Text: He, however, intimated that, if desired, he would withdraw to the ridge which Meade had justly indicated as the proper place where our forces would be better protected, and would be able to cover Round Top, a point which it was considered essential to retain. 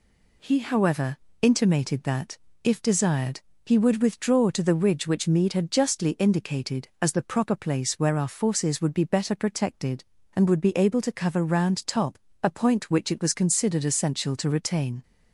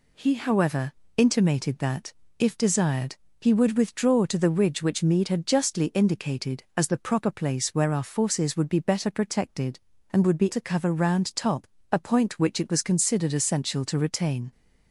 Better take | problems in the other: first | skips "able"; at 10.5 s

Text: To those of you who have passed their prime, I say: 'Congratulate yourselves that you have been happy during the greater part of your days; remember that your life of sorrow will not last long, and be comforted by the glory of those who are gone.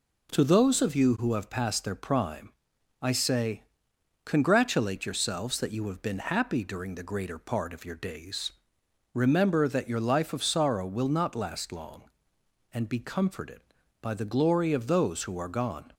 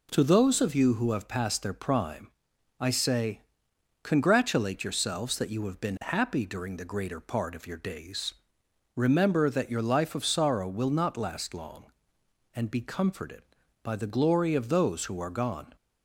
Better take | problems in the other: neither | none

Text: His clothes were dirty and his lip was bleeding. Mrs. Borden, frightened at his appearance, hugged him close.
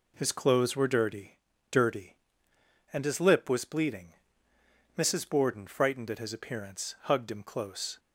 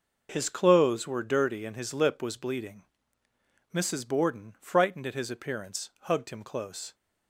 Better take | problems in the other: second | says "dirty" twice; at 1.7 s

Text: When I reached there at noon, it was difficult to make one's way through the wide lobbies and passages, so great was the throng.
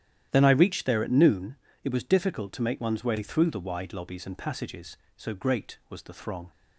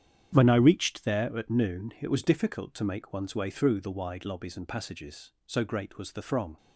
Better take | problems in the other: second | starts louder than the rest; strong; until 1.3 s; 11 dB; strong in the second // says "Then" for "When"; at 0.3 s

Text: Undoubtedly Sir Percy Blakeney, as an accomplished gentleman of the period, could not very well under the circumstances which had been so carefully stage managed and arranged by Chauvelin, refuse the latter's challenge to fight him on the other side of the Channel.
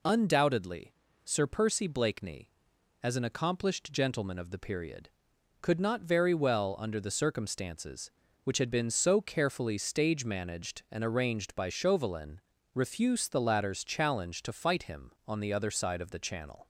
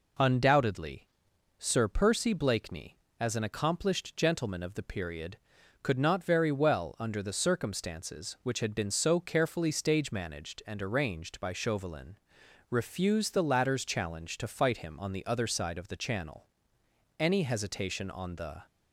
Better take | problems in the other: first | pauses between "Undoubtedly" and "Sir"; noticeable; at 1.0 s; 0.54 s long; slight in the first // goes on to say "Any hesitation on the"; from 17.1 s on; 1.4 s long

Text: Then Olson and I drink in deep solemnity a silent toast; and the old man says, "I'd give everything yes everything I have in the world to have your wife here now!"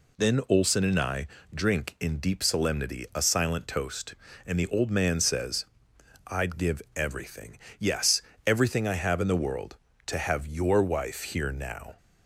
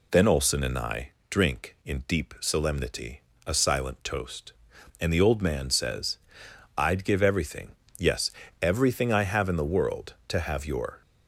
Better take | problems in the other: first | pauses between "I" and "drink"; slight; at 1.0 s; 0.20 s long; slight in the first // pauses between "solemnity" and "a"; slight; at 3.2 s; 0.24 s long // pauses between "everything" and "yes"; slight; at 7.7 s; 0.24 s long; slight in the first // pauses between "yes" and "everything"; slight; at 8.3 s; 0.28 s long; slight in the first // stops before "wife here now"; at 11.0 s

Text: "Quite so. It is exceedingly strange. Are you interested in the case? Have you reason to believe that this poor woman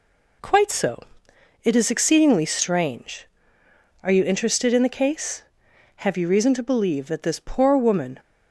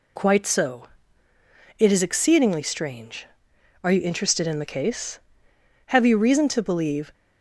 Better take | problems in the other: first | stops before "that this poor woman"; at 7.1 s

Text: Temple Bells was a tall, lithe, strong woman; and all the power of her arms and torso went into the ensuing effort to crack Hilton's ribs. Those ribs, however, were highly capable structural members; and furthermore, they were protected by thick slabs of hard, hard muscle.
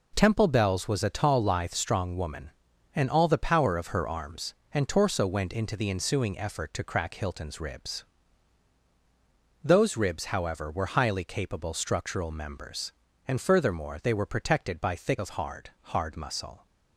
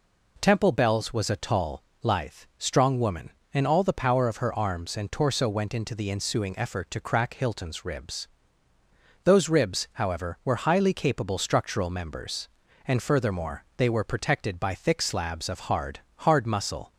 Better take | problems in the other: second | skips "slabs"; at 15.1 s

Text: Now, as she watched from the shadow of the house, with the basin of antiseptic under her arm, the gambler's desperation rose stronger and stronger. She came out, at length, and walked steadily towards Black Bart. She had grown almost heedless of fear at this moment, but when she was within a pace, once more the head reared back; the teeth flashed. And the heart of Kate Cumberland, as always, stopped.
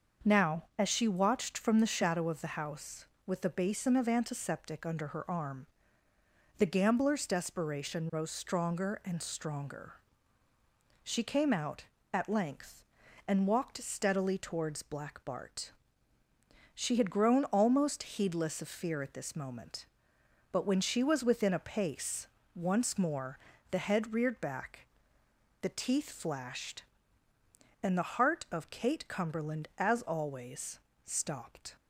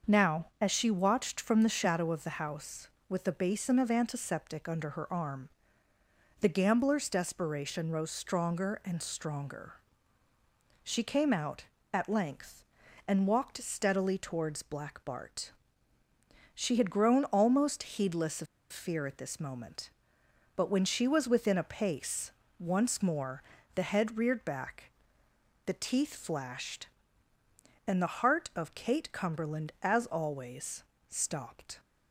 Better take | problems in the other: first | starts louder than the rest; until 1.2 s; 6.5 dB; also in the first // pauses between "of" and "fear"; slight; at 18.4 s; 0.26 s long // pauses between "more" and "the"; slight; at 23.4 s; 0.32 s long; slight in the first

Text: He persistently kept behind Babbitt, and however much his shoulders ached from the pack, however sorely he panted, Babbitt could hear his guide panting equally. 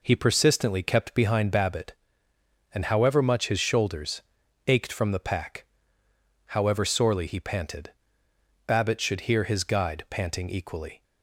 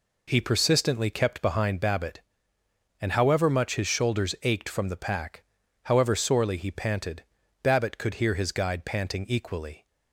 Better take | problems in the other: second | pauses between "shoulders" and "ached"; noticeable; at 4.2 s; 0.46 s long // says "should" for "could"; at 8.9 s

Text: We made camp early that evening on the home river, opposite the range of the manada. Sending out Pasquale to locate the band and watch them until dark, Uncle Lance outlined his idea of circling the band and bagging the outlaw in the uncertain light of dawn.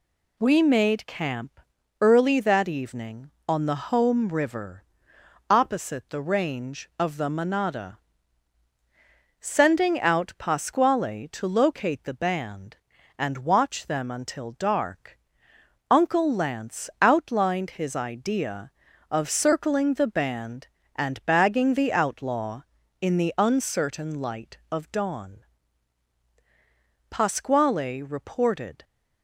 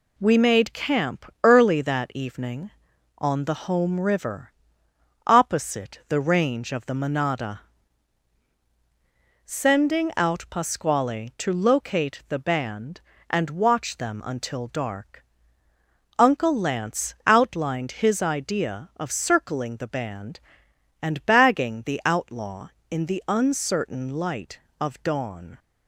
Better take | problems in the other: second | pauses between "camp" and "early"; at 1.5 s; 0.42 s long; slight in the second // goes on to say "Pasquale reported"; strong; from 27.1 s on; 1.7 s long

